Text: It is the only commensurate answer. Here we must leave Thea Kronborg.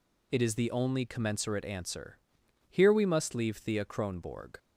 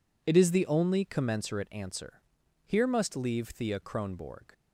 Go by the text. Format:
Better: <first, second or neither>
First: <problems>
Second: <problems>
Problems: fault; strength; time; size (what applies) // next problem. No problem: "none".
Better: first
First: none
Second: skips "we"; at 2.8 s